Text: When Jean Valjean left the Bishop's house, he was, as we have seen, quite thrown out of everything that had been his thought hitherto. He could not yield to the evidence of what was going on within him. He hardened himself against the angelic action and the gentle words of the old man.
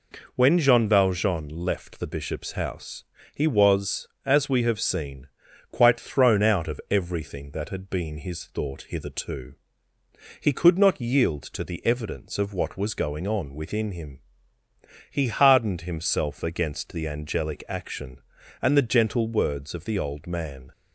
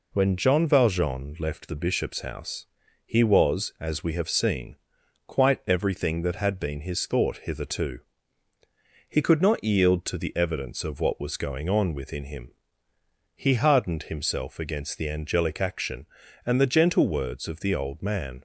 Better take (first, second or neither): first